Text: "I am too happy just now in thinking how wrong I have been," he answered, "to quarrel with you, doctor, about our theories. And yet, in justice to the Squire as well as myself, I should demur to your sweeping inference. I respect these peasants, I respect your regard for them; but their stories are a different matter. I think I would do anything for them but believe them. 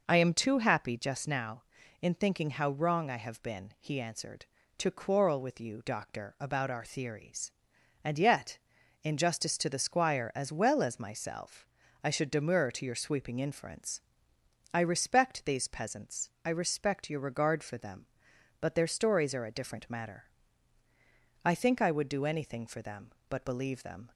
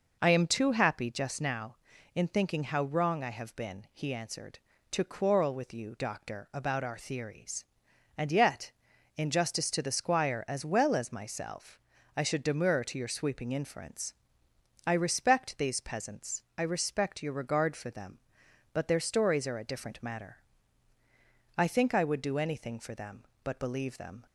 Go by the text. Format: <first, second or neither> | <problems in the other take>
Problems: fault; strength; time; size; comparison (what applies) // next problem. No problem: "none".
neither | none